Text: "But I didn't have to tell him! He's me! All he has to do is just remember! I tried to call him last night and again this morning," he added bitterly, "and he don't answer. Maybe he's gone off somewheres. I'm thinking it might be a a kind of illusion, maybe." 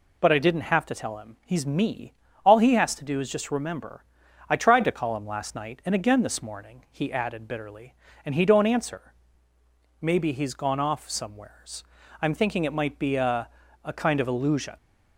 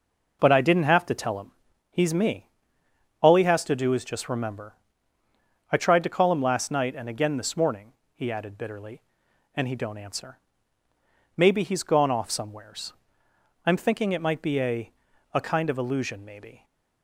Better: second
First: pauses between "a" and "a"; slight; at 13.4 s; 0.36 s long // stops before "maybe"; at 14.7 s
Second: pauses between "a" and "a"; at 14.9 s; 0.42 s long

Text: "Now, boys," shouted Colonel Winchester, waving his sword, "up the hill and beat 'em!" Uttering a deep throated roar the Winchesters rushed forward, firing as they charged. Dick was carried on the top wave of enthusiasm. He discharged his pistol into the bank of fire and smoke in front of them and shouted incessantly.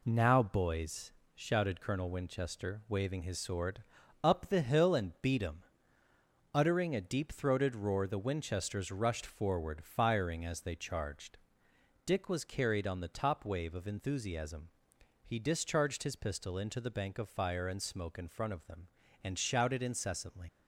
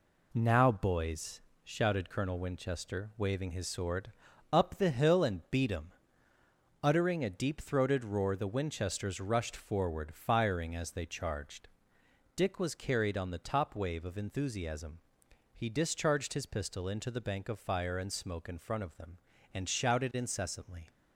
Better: second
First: leaves "incessantly" unfinished; at 20.4 s; 80 ms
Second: none

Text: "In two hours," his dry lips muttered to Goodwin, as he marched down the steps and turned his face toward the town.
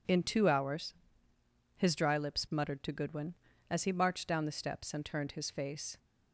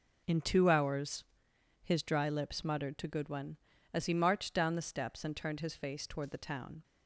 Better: second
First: stops before "toward the town"; at 5.9 s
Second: none

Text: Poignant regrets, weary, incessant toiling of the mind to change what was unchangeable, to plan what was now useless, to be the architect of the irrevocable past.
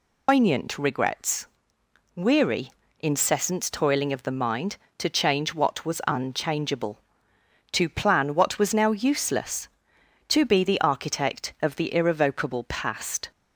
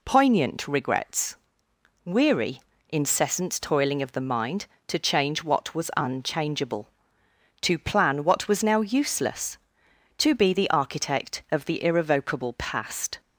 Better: second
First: loses the start of "Poignant"; at 0.2 s; 140 ms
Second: none

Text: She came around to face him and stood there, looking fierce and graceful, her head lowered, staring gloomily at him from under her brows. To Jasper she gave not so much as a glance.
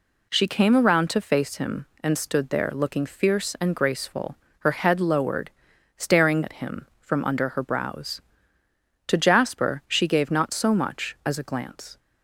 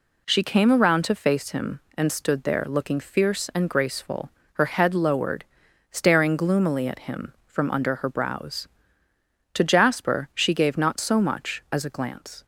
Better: second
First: skips "gloomily"; at 6.4 s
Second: none

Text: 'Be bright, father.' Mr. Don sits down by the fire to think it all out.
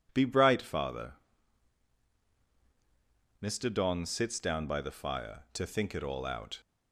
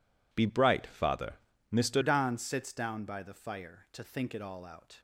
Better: first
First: none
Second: changes voice at "Don"; from 2.0 s on; 3.0 s long

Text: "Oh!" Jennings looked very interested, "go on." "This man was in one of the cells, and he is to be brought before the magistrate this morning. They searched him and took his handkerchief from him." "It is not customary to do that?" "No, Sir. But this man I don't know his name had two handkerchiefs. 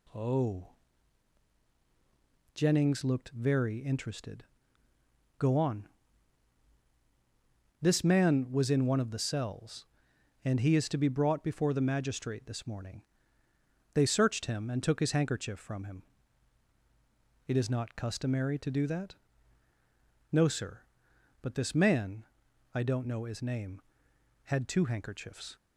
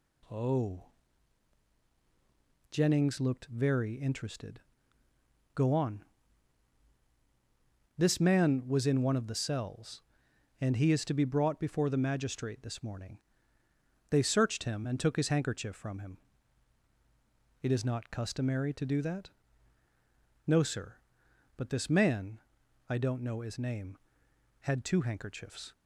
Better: neither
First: pauses between "man" and "I"; noticeable; at 22.2 s; 0.50 s long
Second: pauses between "man" and "I"; noticeable; at 22.3 s; 0.50 s long

